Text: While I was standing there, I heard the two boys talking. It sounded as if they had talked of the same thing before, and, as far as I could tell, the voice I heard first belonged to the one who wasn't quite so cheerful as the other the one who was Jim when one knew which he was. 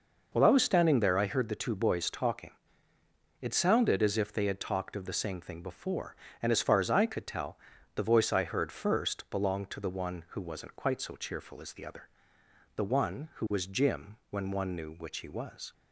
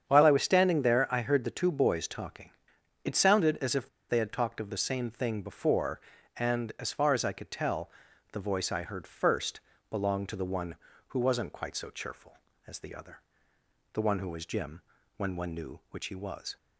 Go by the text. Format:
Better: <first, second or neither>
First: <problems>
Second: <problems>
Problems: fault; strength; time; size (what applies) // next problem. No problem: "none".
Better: first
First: pauses between "other" and "the"; noticeable; at 12.0 s; 0.68 s long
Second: starts louder than the rest; strong; until 1.0 s; 8 dB // pauses between "if" and "they"; slight; at 3.8 s; 0.21 s long // pauses between "first" and "belonged"; slight; at 9.6 s; 0.30 s long // pauses between "other" and "the"; noticeable; at 13.2 s; 0.72 s long // pauses between "Jim" and "when"; at 14.8 s; 0.38 s long